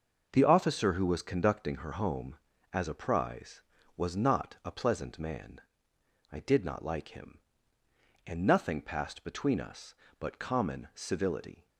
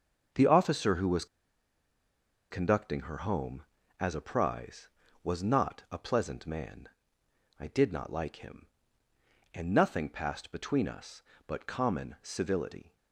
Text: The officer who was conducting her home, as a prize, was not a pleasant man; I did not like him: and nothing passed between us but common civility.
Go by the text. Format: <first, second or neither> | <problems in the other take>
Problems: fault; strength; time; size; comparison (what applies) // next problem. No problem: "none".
first | starts louder than the rest; until 2.5 s; 6 dB; also in the first // pauses between "was" and "conducting"; strong; at 1.2 s; 1.2 s long